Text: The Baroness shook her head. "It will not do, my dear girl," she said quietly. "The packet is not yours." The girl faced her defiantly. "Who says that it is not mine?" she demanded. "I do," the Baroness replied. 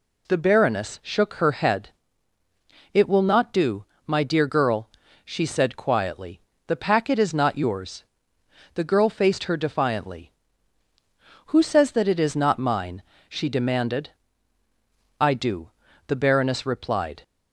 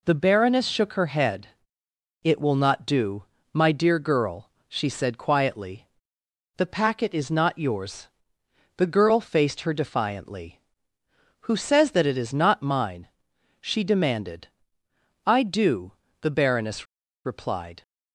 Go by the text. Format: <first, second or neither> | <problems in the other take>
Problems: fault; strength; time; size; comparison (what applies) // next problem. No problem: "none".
first | pauses between "Baroness" and "replied"; at 16.8 s; 0.40 s long